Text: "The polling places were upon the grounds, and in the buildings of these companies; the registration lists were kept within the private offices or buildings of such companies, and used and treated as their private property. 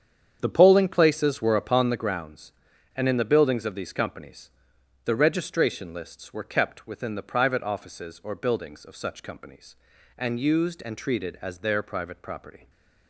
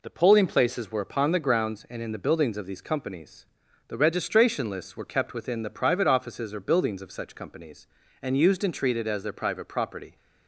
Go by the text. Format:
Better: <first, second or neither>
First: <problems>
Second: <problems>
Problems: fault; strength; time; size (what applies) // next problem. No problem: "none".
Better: second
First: starts louder than the rest; strong; until 2.0 s; 8 dB // stays silent after the last word; slight; from 12.5 s on; 0.5 s long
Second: none